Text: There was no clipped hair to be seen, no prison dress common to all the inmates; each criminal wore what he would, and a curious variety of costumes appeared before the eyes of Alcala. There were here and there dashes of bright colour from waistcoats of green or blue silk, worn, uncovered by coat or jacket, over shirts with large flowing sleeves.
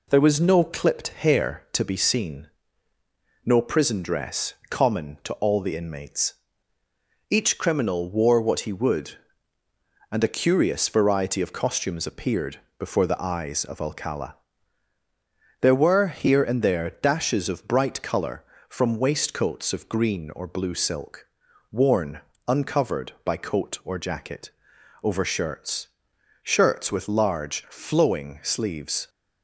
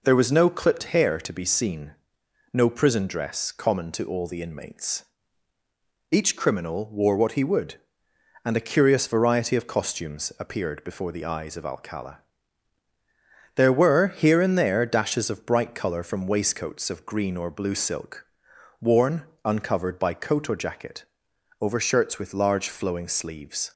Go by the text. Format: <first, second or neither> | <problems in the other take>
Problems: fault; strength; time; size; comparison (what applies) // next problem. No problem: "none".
second | pauses between "dress" and "common"; slight; at 4.5 s; 0.16 s long // pauses between "appeared" and "before"; slight; at 12.5 s; 0.20 s long // says "shirts" twice; at 26.4 s